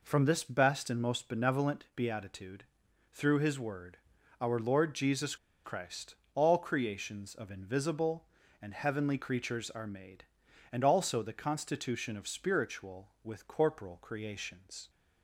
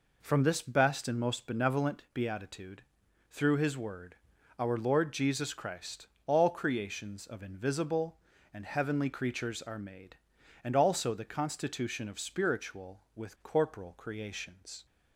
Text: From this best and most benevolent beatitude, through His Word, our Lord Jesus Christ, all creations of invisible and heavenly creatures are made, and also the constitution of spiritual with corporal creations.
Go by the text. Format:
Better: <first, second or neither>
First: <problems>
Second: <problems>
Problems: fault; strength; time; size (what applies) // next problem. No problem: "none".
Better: second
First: pauses between "Jesus" and "Christ"; slight; at 5.3 s; 0.29 s long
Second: none